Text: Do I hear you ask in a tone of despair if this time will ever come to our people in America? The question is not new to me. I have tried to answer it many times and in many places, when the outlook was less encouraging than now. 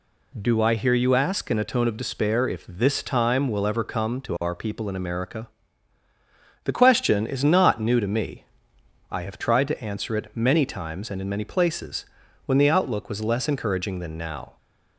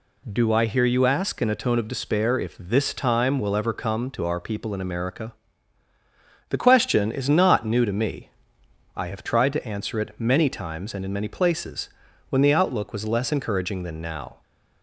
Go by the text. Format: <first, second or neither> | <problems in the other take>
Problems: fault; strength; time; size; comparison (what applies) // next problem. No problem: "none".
neither | none